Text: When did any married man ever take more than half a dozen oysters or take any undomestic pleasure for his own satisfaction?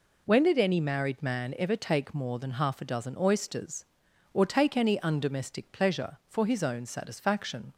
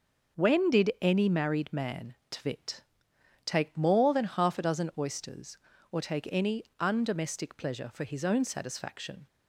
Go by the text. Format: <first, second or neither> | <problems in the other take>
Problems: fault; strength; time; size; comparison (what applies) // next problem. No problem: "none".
first | starts louder than the rest; until 1.4 s; 6 dB // says "tvit" for "ever"; at 2.2 s